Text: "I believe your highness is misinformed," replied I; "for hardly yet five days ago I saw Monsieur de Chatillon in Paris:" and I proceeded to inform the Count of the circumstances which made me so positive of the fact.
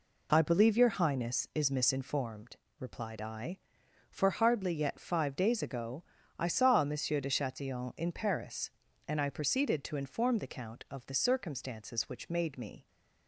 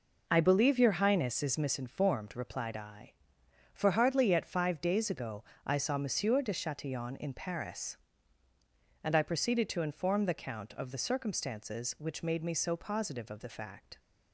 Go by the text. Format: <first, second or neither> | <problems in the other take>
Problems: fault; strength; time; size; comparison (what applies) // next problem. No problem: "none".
second | pauses between "ago" and "I"; slight; at 6.0 s; 0.34 s long; slight in the second // stops before "so positive of the fact"; at 12.8 s